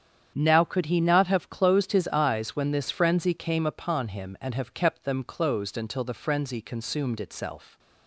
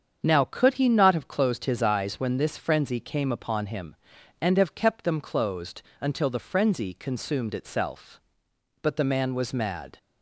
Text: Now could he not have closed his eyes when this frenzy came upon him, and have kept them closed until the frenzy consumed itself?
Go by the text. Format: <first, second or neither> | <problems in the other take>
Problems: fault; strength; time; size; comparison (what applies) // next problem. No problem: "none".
first | starts louder than the rest; strong; until 1.2 s; 7.5 dB; strong in the first // pauses between "closed" and "until"; slight; at 5.8 s; 0.18 s long // goes on to say "But the man was mad"; noticeable; from 8.8 s on; 1.1 s long